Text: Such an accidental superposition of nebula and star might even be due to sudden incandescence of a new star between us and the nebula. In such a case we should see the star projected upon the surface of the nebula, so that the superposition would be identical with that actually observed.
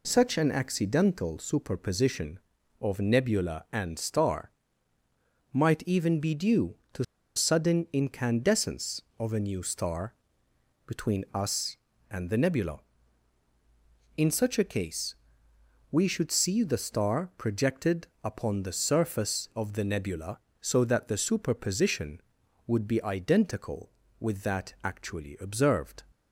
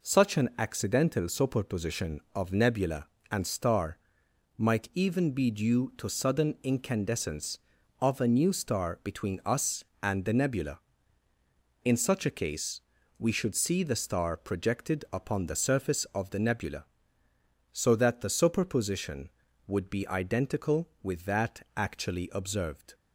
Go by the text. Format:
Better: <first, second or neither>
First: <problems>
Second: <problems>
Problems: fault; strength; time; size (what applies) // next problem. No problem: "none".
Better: second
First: pauses between "star" and "might"; at 4.5 s; 1.0 s long // pauses between "to" and "sudden"; slight; at 7.0 s; 0.32 s long // pauses between "star" and "between"; noticeable; at 10.1 s; 0.72 s long // pauses between "case" and "we"; noticeable; at 15.1 s; 0.76 s long // pauses between "projected" and "upon"; slight; at 18.0 s; 0.18 s long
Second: pauses between "star" and "might"; noticeable; at 3.9 s; 0.58 s long // pauses between "case" and "we"; at 12.7 s; 0.38 s long